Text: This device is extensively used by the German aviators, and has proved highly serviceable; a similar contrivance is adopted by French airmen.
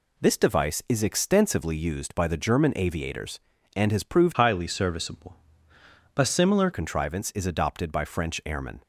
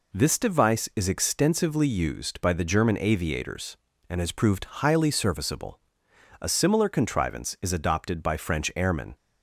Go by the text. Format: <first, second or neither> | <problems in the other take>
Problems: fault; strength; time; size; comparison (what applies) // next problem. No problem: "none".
second | changes voice from "highly" to "similar"; from 4.3 to 6.6 s; 2.3 s long